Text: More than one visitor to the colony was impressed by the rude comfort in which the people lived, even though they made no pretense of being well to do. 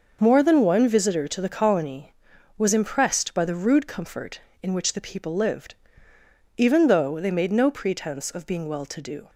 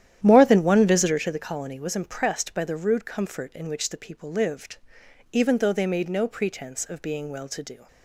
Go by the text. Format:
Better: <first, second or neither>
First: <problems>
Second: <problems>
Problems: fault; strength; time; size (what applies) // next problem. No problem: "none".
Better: first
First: none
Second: starts louder than the rest; strong; until 1.4 s; 11 dB